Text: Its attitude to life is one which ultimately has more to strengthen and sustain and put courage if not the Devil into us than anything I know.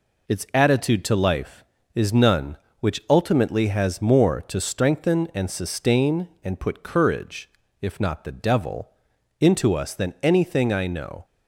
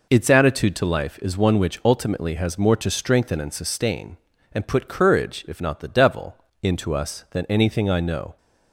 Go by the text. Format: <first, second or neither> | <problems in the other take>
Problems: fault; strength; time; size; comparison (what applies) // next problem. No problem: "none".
second | says "none" for "one"; at 2.1 s // pauses between "courage" and "if"; slight; at 7.4 s; 0.32 s long // pauses between "Devil" and "into"; noticeable; at 8.8 s; 0.52 s long; slight in the second